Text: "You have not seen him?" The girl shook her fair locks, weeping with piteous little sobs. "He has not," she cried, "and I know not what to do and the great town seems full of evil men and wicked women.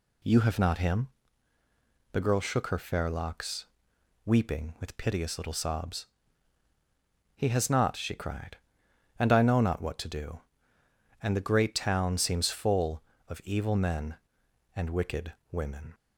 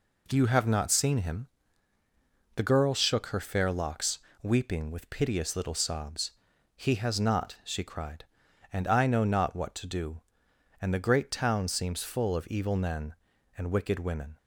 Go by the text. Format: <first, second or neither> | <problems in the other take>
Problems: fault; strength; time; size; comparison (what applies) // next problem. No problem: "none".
second | skips "seen"; at 0.7 s // pauses between "wicked" and "women"; slight; at 15.3 s; 0.22 s long